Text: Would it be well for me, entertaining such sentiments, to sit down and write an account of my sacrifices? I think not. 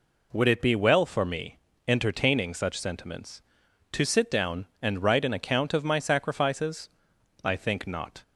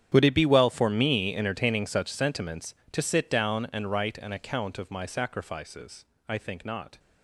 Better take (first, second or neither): first